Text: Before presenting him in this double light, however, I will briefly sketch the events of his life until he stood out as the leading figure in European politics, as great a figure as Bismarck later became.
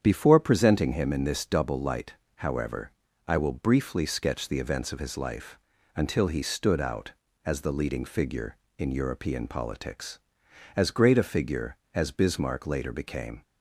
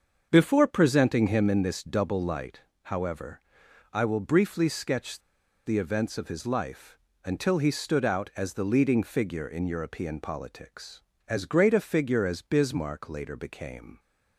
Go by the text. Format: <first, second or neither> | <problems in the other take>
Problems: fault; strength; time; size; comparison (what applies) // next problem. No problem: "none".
first | starts louder than the rest; until 1.3 s; 7 dB; strong in the first // pauses between "sketch" and "the"; at 5.2 s; 0.45 s long // pauses between "life" and "until"; slight; at 6.9 s; 0.26 s long; slight in the first